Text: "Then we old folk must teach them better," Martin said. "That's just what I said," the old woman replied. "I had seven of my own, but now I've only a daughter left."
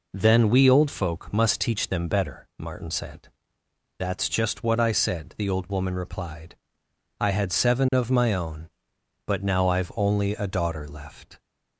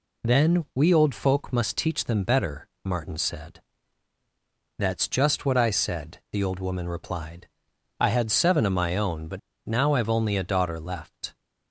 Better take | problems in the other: first | pauses between "but" and "now"; slight; at 9.3 s; 0.27 s long

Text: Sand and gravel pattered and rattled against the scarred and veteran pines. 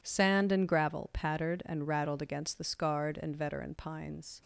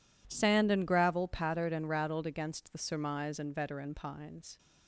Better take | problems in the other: first | says "surmise" for "scarred"; at 2.7 s

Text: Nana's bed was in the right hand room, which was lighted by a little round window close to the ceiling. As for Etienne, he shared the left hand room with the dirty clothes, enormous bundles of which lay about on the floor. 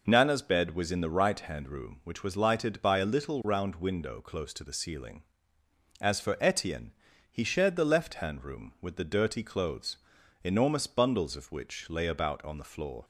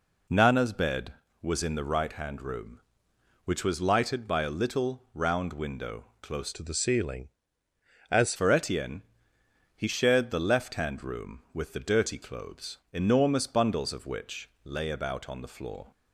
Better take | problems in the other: first | pauses between "window" and "close"; slight; at 6.0 s; 0.16 s long // changes voice from "to" to "As"; from 6.5 to 8.3 s; 1.8 s long

